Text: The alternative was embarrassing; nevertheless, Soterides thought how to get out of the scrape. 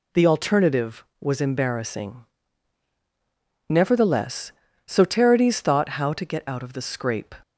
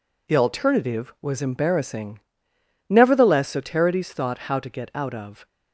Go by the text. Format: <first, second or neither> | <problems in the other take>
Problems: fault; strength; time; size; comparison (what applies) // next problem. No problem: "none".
first | stops before "the scrape"; at 5.4 s